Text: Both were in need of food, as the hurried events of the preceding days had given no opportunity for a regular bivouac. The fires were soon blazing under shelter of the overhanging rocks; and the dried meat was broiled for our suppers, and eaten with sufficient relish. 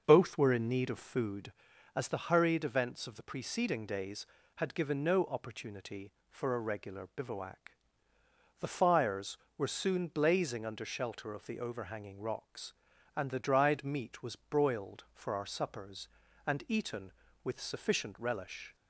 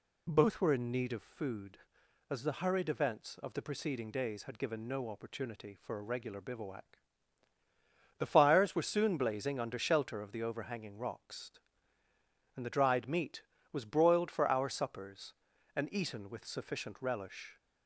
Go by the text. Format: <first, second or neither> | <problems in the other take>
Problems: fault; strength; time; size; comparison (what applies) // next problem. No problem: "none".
second | starts louder than the rest; until 1.5 s; 6 dB